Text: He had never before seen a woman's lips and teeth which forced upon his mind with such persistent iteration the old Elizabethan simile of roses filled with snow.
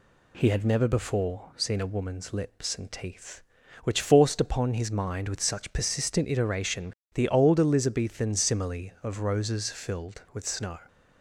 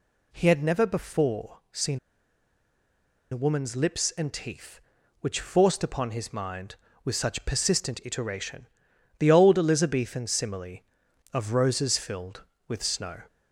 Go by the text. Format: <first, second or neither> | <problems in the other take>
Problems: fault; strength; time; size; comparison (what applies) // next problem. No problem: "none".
first | pauses between "seen" and "a"; strong; at 1.9 s; 1.3 s long // pauses between "iteration" and "the"; noticeable; at 8.6 s; 0.52 s long; slight in the first